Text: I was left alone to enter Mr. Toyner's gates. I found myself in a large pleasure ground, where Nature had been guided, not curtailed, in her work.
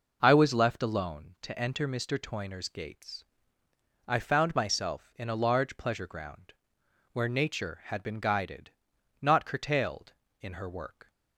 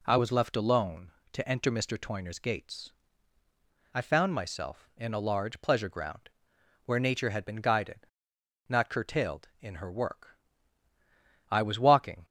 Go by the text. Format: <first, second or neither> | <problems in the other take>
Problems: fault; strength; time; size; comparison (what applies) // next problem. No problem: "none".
first | goes on to say "I was walking"; noticeable; from 11.5 s on; 0.74 s long